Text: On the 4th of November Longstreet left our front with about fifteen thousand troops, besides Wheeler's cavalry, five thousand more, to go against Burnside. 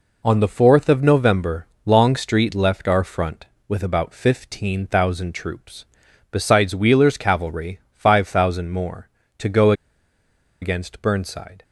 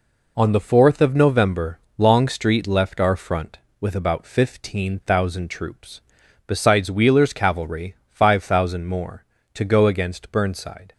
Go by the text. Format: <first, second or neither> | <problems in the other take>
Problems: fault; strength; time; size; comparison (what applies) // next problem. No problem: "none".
second | pauses between "November" and "Longstreet"; slight; at 1.6 s; 0.18 s long; slight in the second // pauses between "go" and "against"; noticeable; at 9.7 s; 0.88 s long